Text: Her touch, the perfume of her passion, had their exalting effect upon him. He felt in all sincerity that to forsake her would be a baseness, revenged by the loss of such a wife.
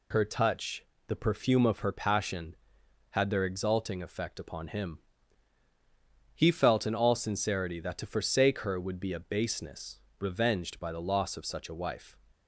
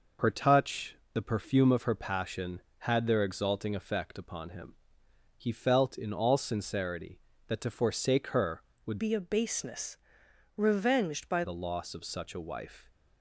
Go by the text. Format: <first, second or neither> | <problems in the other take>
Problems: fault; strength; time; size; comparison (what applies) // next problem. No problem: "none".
first | changes voice from "be" to "by"; from 8.9 to 11.4 s; 2.5 s long